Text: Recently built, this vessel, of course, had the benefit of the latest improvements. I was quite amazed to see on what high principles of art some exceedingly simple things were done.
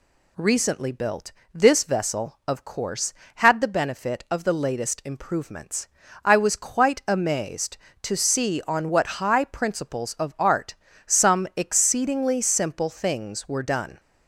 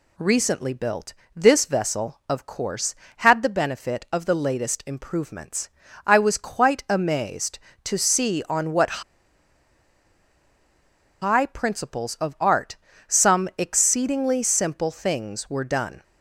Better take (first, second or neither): first